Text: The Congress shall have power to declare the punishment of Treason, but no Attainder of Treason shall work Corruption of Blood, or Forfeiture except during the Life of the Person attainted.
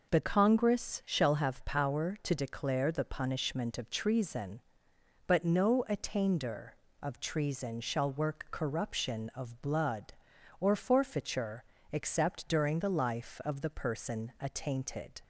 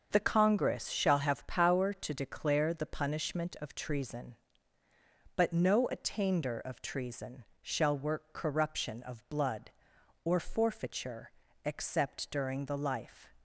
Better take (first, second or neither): first